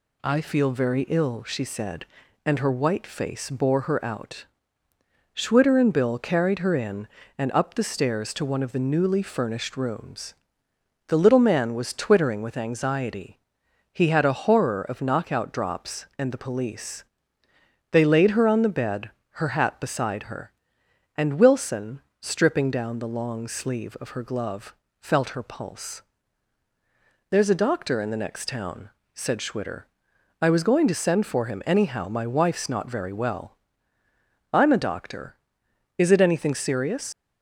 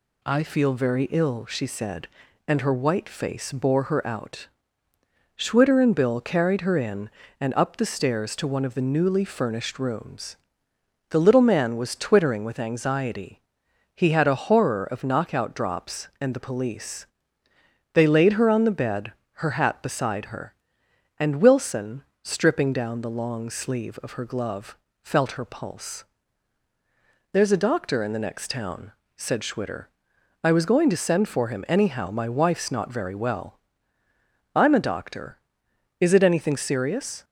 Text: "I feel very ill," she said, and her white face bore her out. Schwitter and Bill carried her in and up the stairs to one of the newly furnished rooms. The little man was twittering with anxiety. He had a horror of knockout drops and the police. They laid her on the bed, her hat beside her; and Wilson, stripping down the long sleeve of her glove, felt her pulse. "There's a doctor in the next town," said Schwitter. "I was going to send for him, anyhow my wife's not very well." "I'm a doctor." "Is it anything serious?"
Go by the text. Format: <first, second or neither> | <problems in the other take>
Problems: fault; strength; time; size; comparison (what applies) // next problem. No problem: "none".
second | leaves "serious" unfinished; at 37.1 s; 90 ms